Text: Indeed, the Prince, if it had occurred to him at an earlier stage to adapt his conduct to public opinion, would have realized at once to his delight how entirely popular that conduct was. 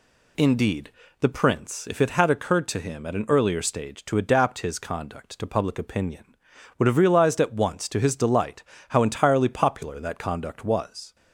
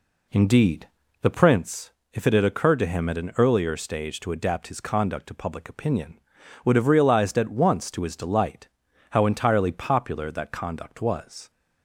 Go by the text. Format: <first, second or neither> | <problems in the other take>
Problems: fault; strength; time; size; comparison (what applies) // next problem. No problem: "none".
first | starts louder than the rest; slight; until 1.7 s; 2.5 dB // pauses between "delight" and "how"; at 8.6 s; 0.44 s long; slight in the first